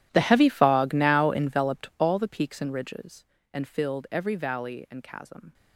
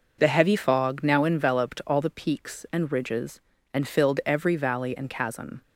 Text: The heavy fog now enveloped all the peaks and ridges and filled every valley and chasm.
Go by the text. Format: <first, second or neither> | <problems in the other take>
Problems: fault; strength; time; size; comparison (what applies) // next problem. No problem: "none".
second | gets quieter; strong; throughout; 21 dB